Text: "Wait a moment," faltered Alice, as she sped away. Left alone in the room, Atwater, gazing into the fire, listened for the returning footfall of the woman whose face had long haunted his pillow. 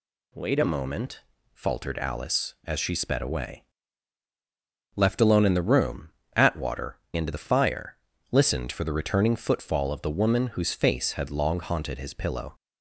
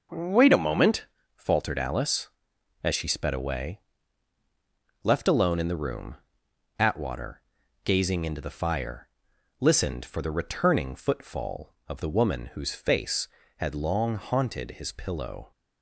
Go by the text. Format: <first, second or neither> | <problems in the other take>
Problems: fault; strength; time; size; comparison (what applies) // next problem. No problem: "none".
second | skips "gazing"; at 7.0 s